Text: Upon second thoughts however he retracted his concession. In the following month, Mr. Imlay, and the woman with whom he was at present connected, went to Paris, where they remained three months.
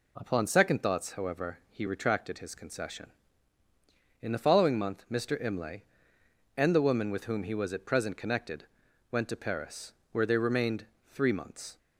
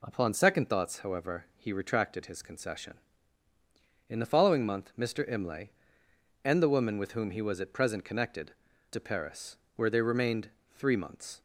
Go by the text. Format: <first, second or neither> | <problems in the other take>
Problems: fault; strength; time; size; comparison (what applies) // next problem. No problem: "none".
first | skips "went"; at 8.7 s // pauses between "remained" and "three"; slight; at 10.4 s; 0.24 s long; slight in the first